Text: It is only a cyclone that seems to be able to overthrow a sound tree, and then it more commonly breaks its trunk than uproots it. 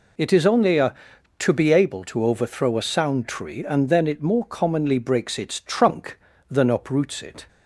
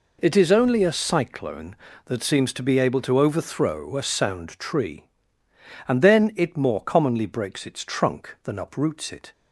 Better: second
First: skips "cyclone that seems"; at 1.1 s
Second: none

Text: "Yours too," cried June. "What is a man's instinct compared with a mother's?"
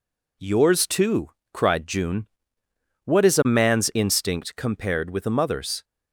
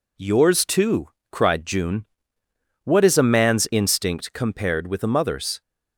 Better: neither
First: none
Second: none

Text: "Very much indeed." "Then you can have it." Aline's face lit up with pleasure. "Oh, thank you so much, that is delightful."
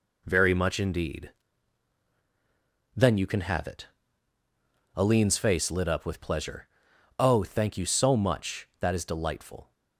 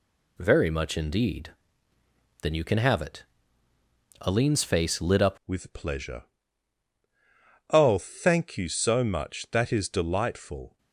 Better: first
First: none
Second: changes voice at "with"; from 5.4 s on; 5.3 s long

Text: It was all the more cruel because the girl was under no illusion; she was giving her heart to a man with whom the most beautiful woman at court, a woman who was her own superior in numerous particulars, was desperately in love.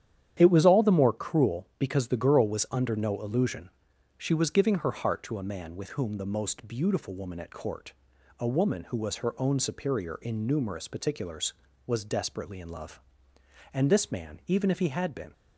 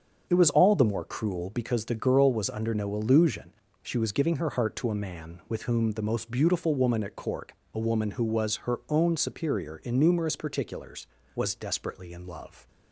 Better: second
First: starts louder than the rest; strong; until 1.3 s; 10 dB // goes on to say "And this man even if he had been"; from 13.7 s on; 1.6 s long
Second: starts louder than the rest; until 1.3 s; 7 dB

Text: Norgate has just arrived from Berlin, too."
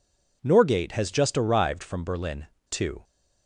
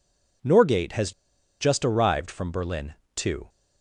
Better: first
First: none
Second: pauses between "has" and "just"; noticeable; at 1.1 s; 0.48 s long

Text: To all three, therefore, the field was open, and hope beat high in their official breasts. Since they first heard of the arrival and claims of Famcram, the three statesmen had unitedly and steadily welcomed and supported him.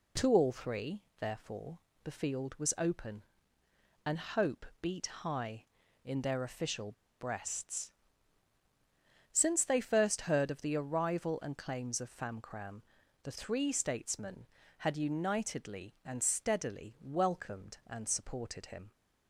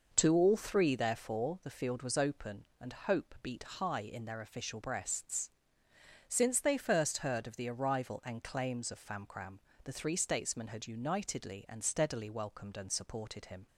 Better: second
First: pauses between "hope" and "beat"; slight; at 4.6 s; 0.16 s long // pauses between "official" and "breasts"; slight; at 6.9 s; 0.25 s long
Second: none

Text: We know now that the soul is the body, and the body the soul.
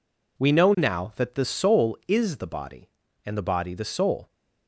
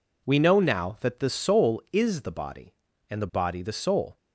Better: neither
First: none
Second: none

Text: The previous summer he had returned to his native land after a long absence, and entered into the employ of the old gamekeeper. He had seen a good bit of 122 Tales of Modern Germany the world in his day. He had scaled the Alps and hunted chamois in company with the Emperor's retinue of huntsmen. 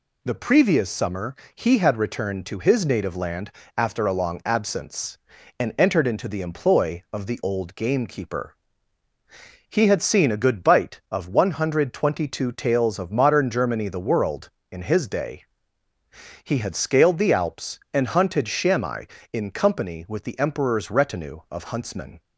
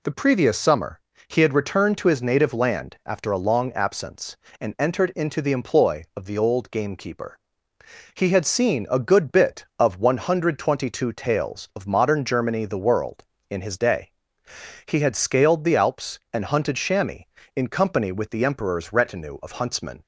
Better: second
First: pauses between "summer" and "he"; slight; at 1.3 s; 0.22 s long // pauses between "land" and "after"; slight; at 3.4 s; 0.26 s long // says "bite" for "bit"; at 10.6 s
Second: pauses between "summer" and "he"; slight; at 0.9 s; 0.28 s long

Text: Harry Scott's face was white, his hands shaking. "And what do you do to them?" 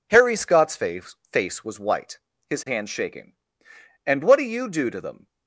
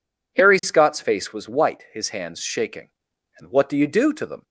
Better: second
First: says "face" twice; at 1.3 s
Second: none

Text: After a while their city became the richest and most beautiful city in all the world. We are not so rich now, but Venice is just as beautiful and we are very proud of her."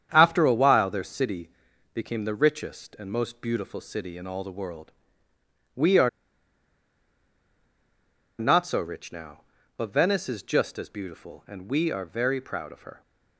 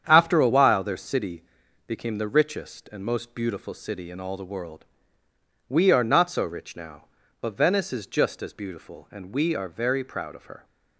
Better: second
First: starts louder than the rest; strong; until 1.1 s; 8.5 dB // pauses between "city" and "became"; at 1.4 s; 0.44 s long // pauses between "are" and "not"; strong; at 6.0 s; 2.2 s long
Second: starts louder than the rest; strong; until 1.0 s; 8.5 dB // pauses between "city" and "became"; at 1.4 s; 0.44 s long

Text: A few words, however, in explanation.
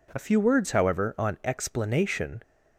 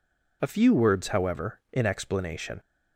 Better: second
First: says "on" for "in"; at 1.1 s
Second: none

